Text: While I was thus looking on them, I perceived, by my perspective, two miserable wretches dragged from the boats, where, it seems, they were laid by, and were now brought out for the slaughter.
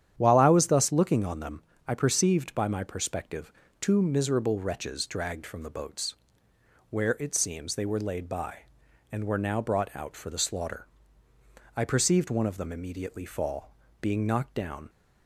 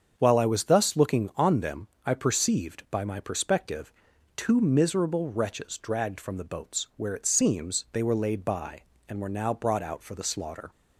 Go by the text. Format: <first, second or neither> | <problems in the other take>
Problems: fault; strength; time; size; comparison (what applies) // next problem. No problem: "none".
second | starts louder than the rest; strong; until 1.1 s; 9.5 dB; strong in the second // goes on to say "I perceived one of them immediately fall being knocked down"; strong; from 11.7 s on; 3.1 s long